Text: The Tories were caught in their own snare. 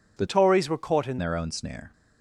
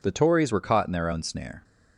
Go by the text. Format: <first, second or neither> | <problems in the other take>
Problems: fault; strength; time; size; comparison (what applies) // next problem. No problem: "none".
second | changes voice from "Tories" to "in"; from 0.2 to 1.1 s; 0.9 s long